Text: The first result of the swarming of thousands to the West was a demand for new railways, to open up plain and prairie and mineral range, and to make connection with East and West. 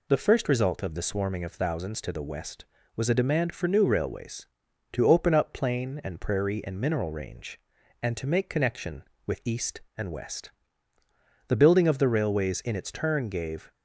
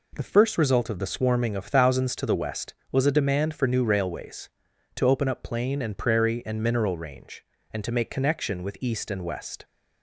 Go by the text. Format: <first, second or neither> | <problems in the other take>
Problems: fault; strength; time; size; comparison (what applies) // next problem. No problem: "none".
second | goes on to say "The building of the railways in its turn gave"; strong; from 11.4 s on; 2.2 s long